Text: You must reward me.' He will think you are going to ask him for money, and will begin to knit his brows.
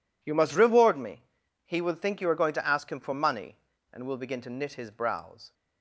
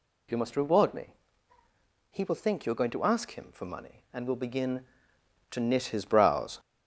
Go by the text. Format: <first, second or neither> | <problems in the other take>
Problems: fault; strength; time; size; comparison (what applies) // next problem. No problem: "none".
first | gets louder; throughout; 4 dB